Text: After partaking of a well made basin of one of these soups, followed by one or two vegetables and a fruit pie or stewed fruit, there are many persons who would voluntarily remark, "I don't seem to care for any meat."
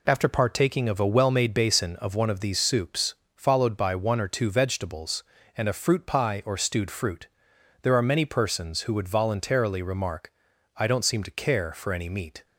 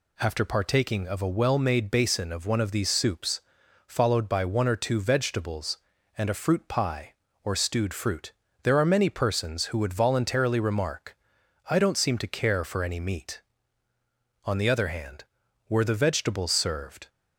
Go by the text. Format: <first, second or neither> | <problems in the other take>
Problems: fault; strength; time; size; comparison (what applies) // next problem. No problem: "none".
first | goes on to say "On the other hand were the vegetables served"; strong; from 14.4 s on; 2.6 s long